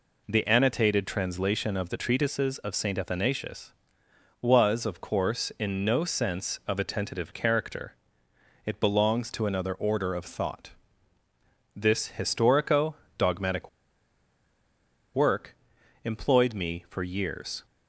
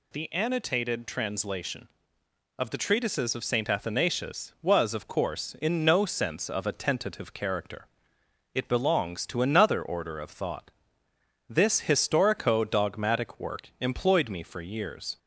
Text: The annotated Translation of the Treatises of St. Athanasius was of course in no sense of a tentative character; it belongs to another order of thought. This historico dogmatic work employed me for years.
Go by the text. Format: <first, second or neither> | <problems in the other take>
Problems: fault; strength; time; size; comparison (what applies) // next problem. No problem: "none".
second | pauses between "historico" and "dogmatic"; slight; at 12.9 s; 0.24 s long // pauses between "dogmatic" and "work"; strong; at 13.6 s; 1.4 s long // pauses between "work" and "employed"; noticeable; at 15.5 s; 0.48 s long